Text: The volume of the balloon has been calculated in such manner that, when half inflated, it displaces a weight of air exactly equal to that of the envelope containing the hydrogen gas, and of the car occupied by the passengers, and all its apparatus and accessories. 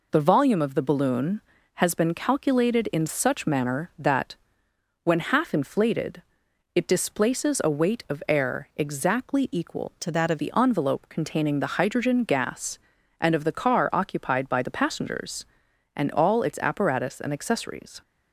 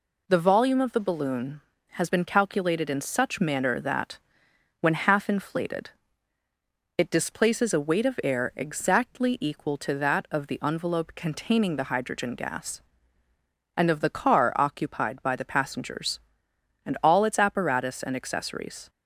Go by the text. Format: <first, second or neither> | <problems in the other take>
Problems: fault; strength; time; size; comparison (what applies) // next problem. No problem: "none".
second | changes voice from "to" to "of"; from 9.9 to 10.3 s; 0.4 s long